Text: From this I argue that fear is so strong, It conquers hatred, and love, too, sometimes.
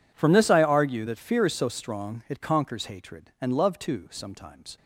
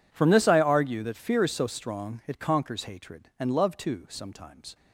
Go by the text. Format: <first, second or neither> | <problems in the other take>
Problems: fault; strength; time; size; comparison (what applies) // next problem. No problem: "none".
neither | none